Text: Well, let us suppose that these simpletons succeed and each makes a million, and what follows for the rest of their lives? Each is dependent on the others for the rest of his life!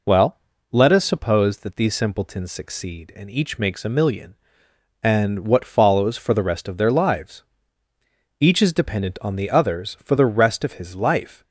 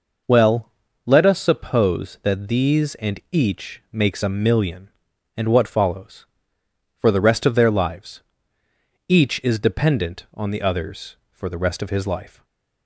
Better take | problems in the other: first | skips "simpletons succeed"; at 2.9 s // stays silent after the last word; slight; from 12.2 s on; 0.6 s long

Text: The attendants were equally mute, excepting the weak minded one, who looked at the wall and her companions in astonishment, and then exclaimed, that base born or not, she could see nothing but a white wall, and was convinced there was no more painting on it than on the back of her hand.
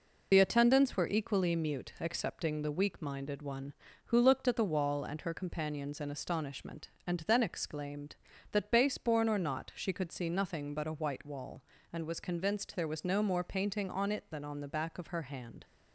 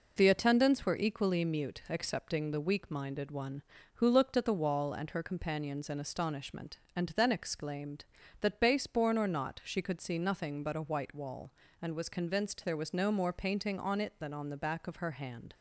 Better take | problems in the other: second | loses the start of "The"; at 0.3 s; 45 ms

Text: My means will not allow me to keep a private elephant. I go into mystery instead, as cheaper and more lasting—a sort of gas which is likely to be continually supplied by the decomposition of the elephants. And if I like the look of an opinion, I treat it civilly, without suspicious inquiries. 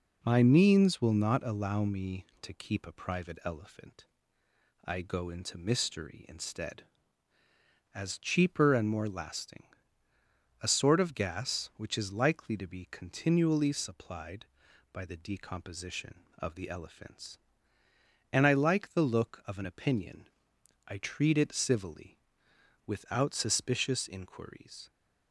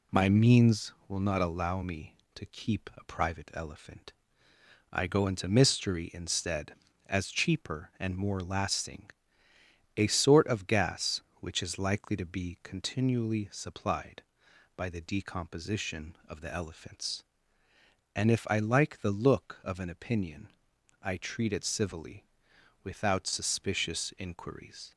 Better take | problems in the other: second | skips "if"; at 18.4 s

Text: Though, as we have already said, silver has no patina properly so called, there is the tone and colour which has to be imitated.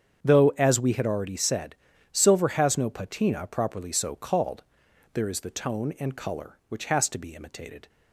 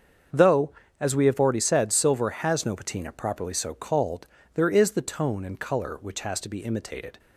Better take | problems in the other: second | starts louder than the rest; strong; until 1.2 s; 8 dB; also in the second // says "had" for "have"; at 0.9 s

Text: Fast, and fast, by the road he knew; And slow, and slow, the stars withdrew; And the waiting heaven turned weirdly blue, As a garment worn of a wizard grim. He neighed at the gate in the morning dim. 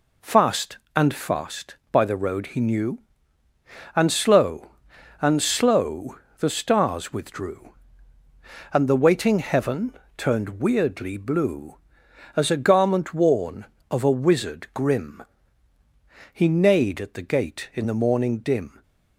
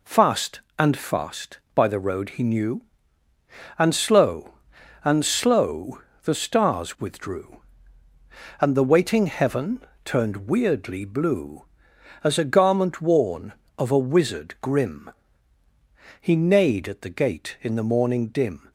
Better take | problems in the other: neither | pauses between "heaven" and "turned"; slight; the same in both

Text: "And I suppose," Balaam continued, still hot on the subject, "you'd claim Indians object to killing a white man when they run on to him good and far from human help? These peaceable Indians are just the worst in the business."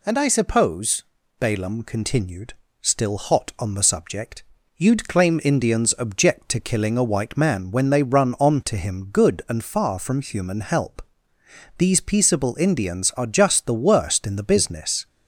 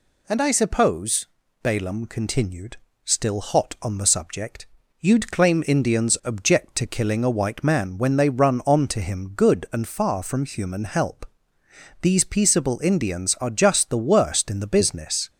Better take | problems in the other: neither | none

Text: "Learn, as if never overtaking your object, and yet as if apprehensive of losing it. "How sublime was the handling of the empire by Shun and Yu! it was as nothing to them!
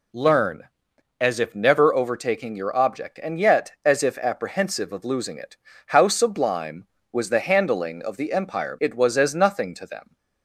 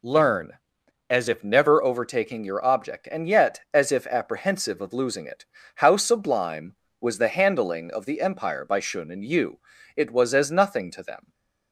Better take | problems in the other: second | skips "by Shun and Yu"; at 8.7 s

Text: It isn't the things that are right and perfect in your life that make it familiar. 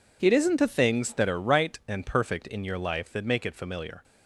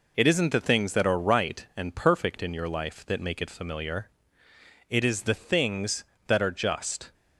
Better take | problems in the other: first | goes on to say "It is the things that are just"; strong; from 4.8 s on; 2.2 s long

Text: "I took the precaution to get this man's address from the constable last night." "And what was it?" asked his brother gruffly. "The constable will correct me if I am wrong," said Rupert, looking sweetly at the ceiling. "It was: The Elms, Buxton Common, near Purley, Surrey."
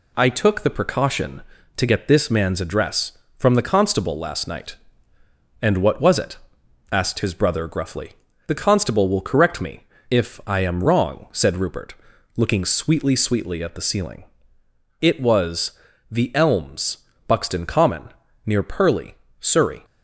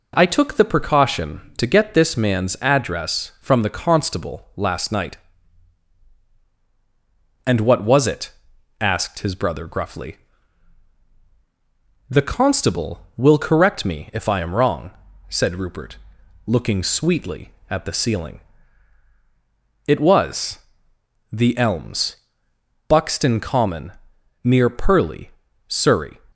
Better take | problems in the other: second | pauses between "me" and "if"; slight; at 9.8 s; 0.26 s long // says "sweetly" twice; at 13.1 s

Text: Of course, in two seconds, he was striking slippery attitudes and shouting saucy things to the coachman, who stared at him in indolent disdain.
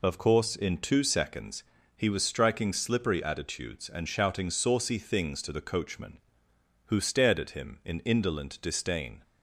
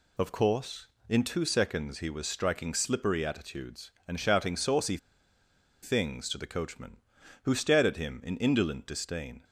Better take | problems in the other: first | pauses between "saucy" and "things"; noticeable; at 4.9 s; 0.85 s long

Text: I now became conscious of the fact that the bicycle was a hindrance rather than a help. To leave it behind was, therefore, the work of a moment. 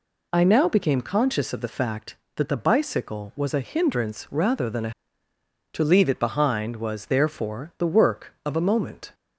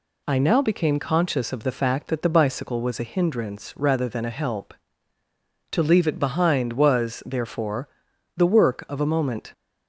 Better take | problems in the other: second | skips "help"; at 5.3 s

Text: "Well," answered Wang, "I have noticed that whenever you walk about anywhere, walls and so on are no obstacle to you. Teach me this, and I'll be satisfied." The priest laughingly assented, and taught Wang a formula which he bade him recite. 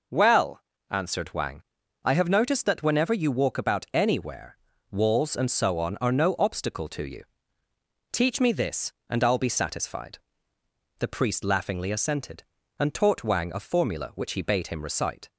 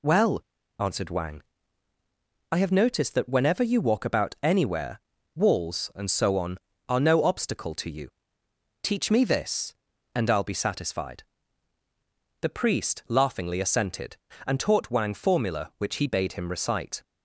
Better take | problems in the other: first | skips "a"; at 15.1 s

